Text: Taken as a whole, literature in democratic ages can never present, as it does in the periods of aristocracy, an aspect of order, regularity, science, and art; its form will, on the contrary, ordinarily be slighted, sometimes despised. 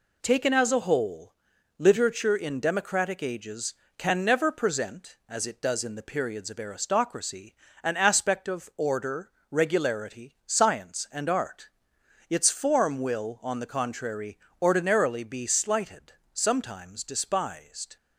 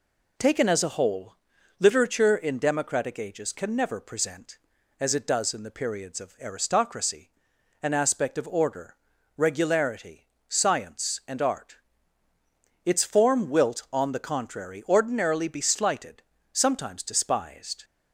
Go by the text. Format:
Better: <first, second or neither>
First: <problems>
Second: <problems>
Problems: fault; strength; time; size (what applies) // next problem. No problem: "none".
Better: first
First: none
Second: says "wilt" for "will"; at 13.4 s